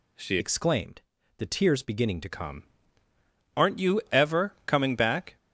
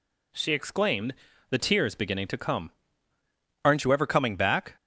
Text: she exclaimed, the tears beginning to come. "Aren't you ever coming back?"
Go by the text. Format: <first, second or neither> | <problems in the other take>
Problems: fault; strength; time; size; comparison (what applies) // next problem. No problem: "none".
second | changes voice from "exclaimed" to "to"; from 0.3 to 2.2 s; 1.9 s long